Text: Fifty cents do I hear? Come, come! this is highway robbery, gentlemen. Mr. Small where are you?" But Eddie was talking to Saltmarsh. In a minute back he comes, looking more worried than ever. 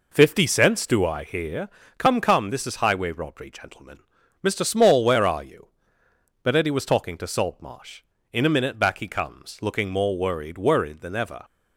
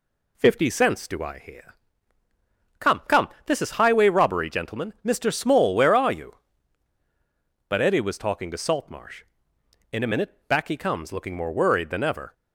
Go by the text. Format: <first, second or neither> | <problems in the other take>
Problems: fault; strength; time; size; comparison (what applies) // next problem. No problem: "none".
second | says "worried" twice; at 10.5 s